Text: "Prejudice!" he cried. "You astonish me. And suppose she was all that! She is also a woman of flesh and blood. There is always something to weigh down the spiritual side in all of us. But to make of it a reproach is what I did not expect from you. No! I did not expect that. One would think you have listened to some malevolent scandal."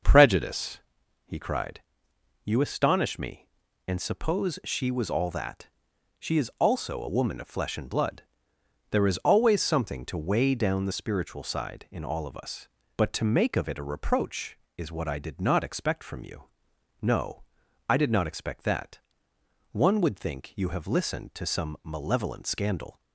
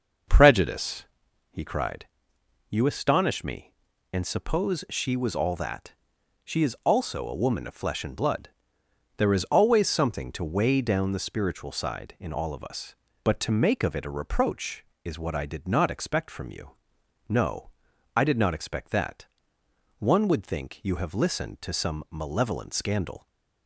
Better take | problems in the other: neither | none

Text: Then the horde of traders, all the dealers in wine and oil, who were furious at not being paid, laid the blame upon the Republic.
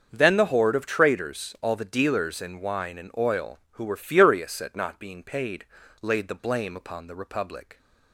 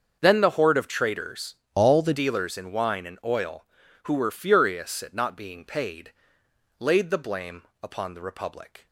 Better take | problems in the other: first | starts louder than the rest; until 1.2 s; 6.5 dB; also in the first // changes voice from "all" to "the"; from 1.7 to 2.1 s; 0.4 s long // pauses between "blame" and "upon"; slight; at 7.6 s; 0.20 s long

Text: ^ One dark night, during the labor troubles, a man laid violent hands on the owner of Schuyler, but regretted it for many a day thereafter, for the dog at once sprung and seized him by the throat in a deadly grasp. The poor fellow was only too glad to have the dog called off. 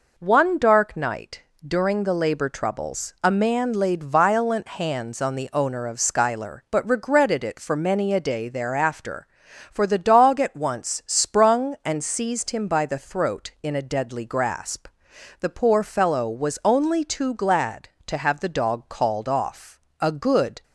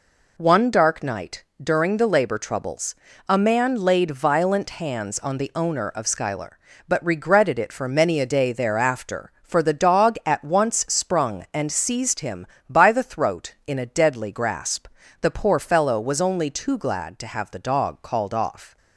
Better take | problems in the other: second | goes on to say "A good"; noticeable; from 20.0 s on; 0.62 s long

